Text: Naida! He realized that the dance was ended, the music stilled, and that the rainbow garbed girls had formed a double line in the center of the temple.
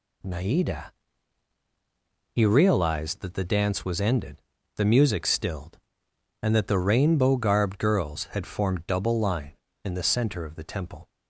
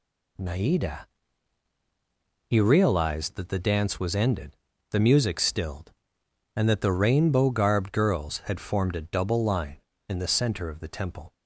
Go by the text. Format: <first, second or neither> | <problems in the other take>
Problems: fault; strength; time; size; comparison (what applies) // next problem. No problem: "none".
second | skips "a"; at 8.7 s